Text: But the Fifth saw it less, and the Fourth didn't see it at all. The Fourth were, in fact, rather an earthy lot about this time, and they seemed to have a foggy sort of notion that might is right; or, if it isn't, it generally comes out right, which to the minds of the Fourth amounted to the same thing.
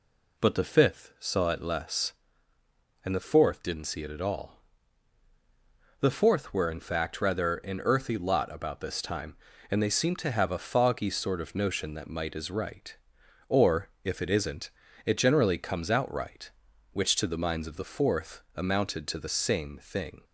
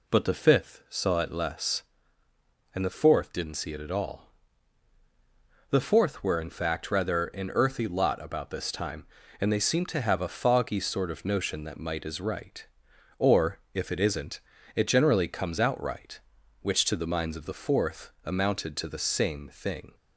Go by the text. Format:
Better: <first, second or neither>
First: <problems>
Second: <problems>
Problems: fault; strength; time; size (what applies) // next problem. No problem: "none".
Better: neither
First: none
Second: none